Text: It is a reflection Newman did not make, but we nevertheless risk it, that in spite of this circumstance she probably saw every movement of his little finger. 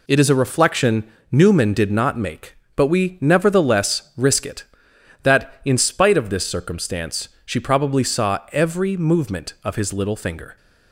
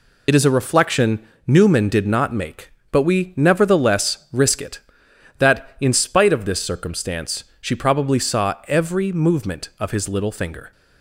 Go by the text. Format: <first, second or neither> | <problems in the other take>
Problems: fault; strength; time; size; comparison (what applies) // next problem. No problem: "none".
first | loses the start of "It"; at 0.2 s; 50 ms // pauses between "reflection" and "Newman"; slight; at 1.2 s; 0.22 s long; slight in the first // pauses between "circumstance" and "she"; slight; at 7.4 s; 0.16 s long; slight in the first